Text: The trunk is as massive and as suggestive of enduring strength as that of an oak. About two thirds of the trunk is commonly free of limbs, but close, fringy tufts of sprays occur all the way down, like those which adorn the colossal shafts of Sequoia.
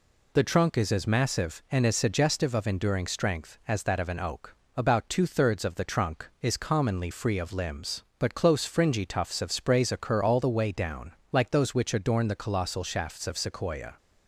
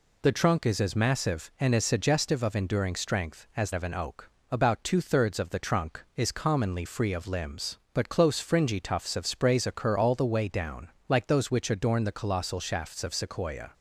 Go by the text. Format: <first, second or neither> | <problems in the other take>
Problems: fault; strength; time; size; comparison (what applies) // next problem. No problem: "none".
first | skips "that"; at 3.7 s